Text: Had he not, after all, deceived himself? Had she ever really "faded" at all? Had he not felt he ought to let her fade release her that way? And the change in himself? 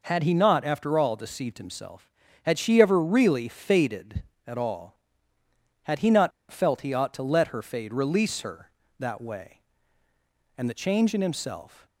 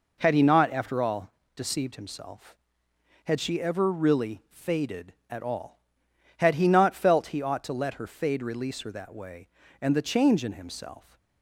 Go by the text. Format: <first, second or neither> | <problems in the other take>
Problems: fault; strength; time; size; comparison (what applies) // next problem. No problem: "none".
second | pauses between "not" and "felt"; slight; at 6.3 s; 0.20 s long